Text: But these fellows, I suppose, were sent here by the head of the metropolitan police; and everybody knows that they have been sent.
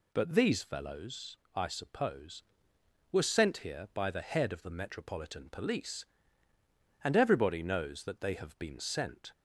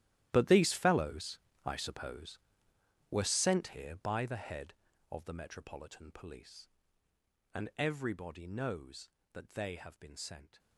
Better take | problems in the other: first | gets quieter; strong; throughout; 16 dB

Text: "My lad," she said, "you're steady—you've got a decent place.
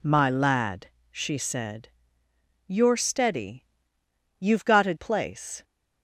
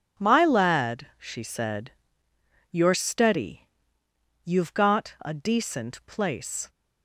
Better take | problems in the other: second | skips "decent"; at 4.9 s

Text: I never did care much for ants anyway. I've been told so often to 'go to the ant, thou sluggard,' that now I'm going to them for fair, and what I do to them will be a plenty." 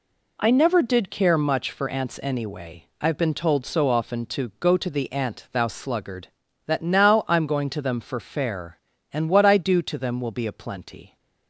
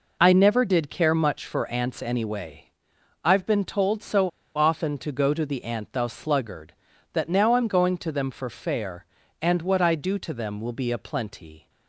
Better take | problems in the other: first | pauses between "so" and "often"; slight; at 4.2 s; 0.27 s long

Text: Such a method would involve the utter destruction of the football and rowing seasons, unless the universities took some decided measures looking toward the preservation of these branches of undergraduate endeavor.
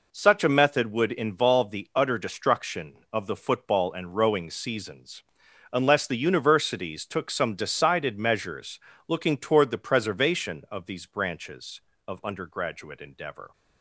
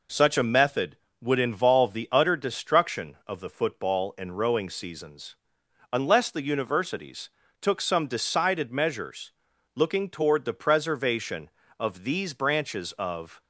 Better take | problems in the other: first | pauses between "universities" and "took"; slight; at 7.2 s; 0.32 s long // pauses between "measures" and "looking"; noticeable; at 9.3 s; 0.46 s long; slight in the first // stops before "undergraduate endeavor"; at 13.4 s

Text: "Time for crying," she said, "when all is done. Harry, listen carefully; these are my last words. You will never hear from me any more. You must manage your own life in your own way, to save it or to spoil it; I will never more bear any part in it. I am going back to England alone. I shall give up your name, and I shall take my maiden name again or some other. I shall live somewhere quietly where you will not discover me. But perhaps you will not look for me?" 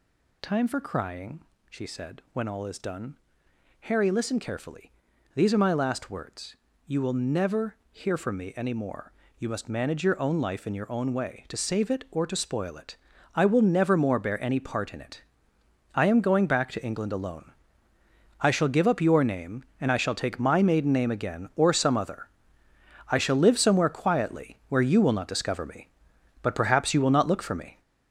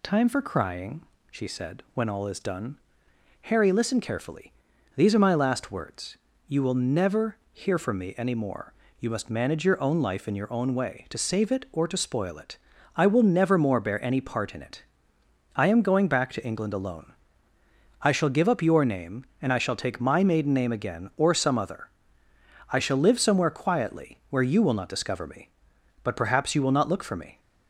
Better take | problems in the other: second | gets louder; throughout; 7 dB // pauses between "never" and "hear"; slight; at 7.7 s; 0.16 s long; slight in the second

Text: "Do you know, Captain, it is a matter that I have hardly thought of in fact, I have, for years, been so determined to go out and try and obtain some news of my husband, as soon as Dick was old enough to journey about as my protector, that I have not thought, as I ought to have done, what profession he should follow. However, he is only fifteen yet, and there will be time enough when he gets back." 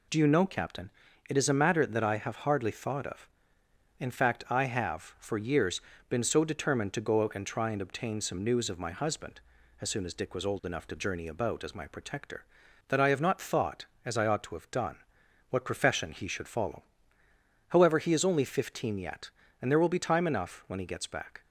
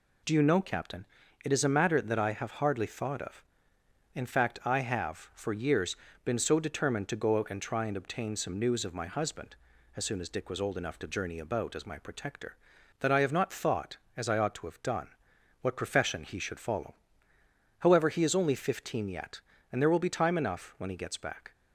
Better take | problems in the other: neither | none

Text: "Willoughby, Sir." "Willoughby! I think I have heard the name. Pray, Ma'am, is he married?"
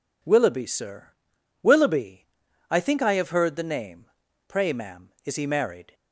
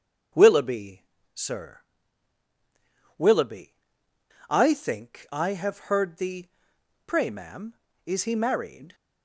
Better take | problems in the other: first | starts louder than the rest; until 1.6 s; 7 dB // skips "name"; at 6.7 s

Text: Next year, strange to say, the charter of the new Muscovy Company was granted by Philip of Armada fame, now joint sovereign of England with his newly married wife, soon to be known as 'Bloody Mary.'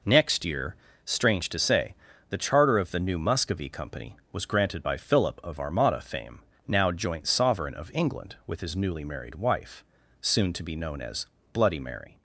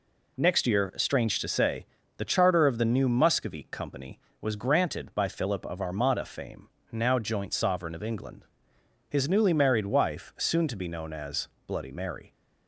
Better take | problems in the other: first | skips "with"; at 8.7 s // pauses between "as" and "Bloody"; slight; at 11.4 s; 0.18 s long; slight in the first

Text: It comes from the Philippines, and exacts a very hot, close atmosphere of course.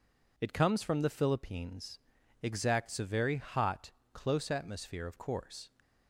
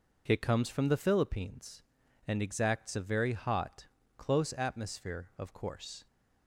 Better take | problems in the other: second | skips "and"; at 2.2 s

